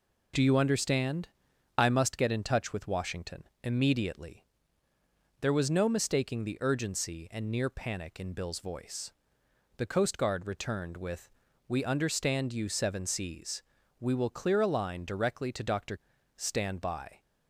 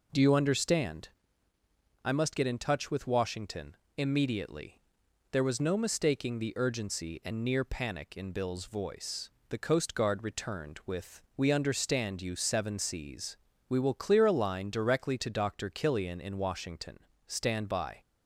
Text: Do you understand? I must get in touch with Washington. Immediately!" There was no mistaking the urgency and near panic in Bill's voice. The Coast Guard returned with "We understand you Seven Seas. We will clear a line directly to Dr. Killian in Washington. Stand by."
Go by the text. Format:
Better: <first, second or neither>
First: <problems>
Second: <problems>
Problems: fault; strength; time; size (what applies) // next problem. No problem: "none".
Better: second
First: pauses between "with" and "We"; at 11.3 s; 0.38 s long // skips "Killian in Washington"; at 16.1 s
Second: pauses between "with" and "We"; slight; at 11.2 s; 0.16 s long